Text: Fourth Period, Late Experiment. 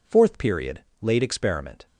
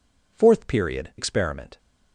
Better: first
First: none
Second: skips "Late"; at 1.1 s

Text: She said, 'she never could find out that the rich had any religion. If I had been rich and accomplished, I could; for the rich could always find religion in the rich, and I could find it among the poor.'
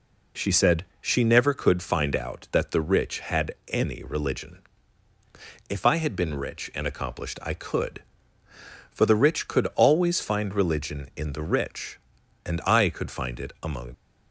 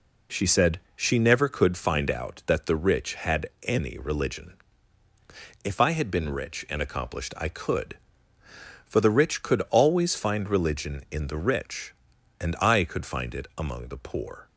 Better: second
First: stops before "the poor"; at 13.9 s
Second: none

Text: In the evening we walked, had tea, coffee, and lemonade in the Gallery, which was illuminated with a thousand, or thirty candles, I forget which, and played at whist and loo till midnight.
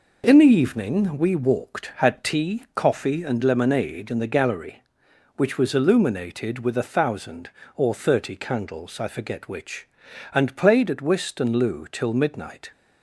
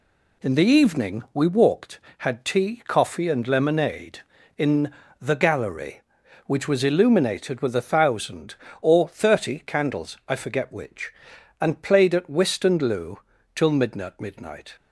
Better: first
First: none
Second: pauses between "in" and "the"; slight; at 4.9 s; 0.28 s long // pauses between "loo" and "till"; at 13.1 s; 0.38 s long // says "midnight" twice; at 14.2 s

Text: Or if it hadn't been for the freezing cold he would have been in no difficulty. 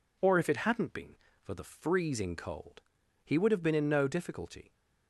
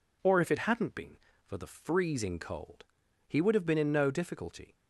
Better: neither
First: pauses between "cold" and "he"; at 2.8 s; 0.42 s long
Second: pauses between "cold" and "he"; at 2.8 s; 0.42 s long

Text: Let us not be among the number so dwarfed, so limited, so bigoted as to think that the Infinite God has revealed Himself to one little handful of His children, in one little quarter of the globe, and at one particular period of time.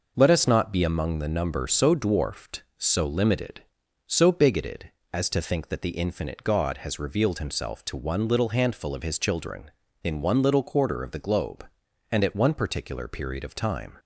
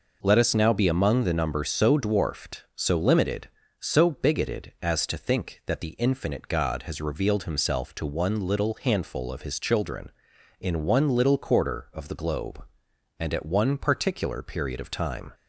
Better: first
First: none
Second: says "now" for "not"; at 0.5 s

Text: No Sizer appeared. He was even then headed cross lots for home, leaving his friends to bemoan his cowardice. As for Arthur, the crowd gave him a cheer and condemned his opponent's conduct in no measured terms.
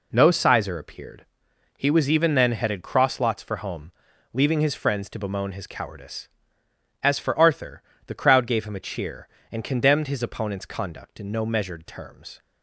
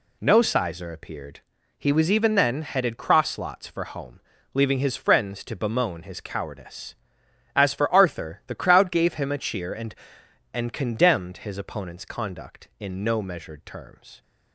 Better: first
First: none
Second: says "and" twice; at 10.5 s

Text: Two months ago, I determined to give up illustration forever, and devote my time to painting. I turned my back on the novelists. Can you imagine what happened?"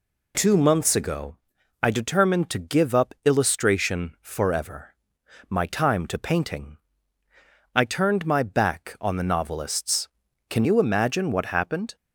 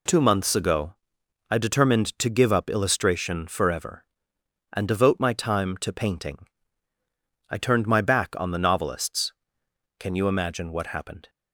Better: second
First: skips "and devote"; at 5.2 s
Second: none

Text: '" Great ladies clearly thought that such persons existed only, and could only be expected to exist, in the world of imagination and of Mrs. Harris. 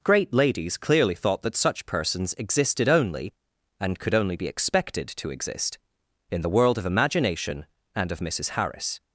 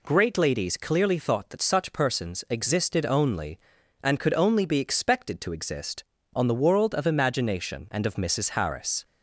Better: first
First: none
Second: says "on" for "in"; at 6.3 s

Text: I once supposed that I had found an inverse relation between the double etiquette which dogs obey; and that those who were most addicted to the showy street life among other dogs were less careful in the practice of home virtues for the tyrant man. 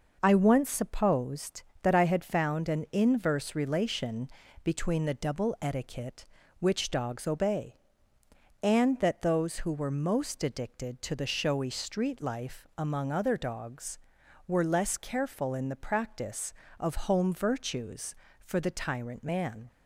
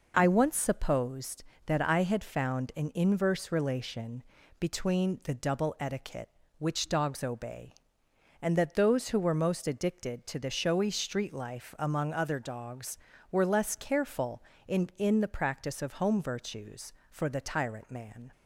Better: first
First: pauses between "relation" and "between"; slight; at 4.2 s; 0.36 s long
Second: pauses between "relation" and "between"; at 4.2 s; 0.38 s long // says "in" twice; at 14.9 s

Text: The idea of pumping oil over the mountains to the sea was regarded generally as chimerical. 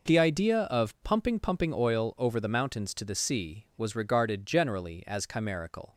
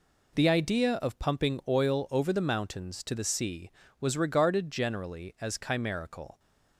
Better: second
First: says "pumping" twice; at 1.4 s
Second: none

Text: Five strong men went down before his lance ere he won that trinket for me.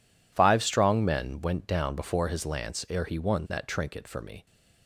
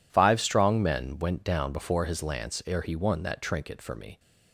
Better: neither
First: none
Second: none

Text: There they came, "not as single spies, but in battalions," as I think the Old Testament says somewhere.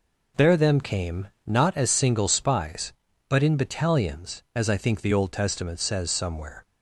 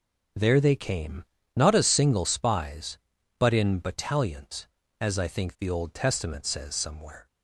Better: second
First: says "them" for "they"; at 0.5 s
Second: none

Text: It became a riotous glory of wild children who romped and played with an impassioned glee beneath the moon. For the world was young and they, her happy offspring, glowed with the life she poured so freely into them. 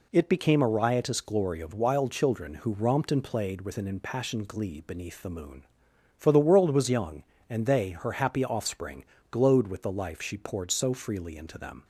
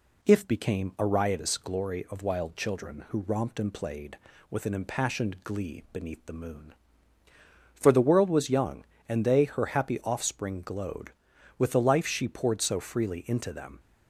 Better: first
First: none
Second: says "If" for "It"; at 0.2 s

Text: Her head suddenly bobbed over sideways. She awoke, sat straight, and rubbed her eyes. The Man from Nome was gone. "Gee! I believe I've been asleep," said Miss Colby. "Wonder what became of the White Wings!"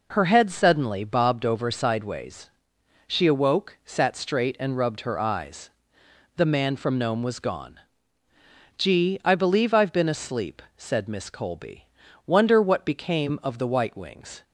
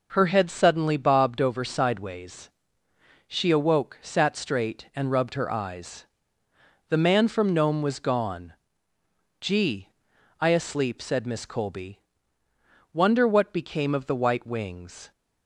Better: first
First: none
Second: skips "believe I've been"; at 10.4 s

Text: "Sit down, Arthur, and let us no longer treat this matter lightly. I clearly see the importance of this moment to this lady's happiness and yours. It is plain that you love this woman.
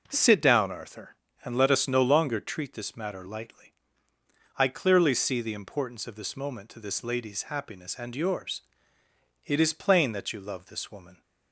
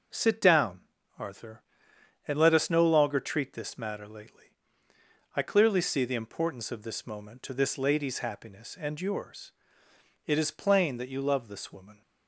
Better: first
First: none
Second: says "lately" for "lightly"; at 4.0 s

